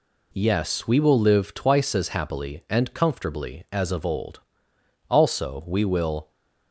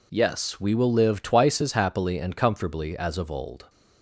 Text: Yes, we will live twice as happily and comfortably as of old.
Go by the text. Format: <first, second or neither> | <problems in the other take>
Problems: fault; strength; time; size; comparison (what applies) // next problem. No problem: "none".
second | goes on to say "Also we will"; noticeable; from 5.0 s on; 1.2 s long